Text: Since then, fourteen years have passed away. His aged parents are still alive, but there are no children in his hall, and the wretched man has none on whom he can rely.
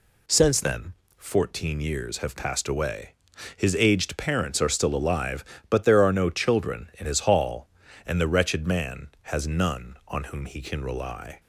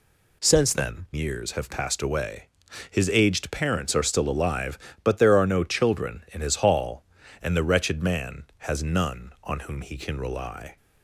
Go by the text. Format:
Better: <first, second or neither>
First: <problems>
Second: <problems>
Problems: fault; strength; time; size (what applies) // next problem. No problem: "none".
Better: first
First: none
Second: skips "fourteen"; at 1.1 s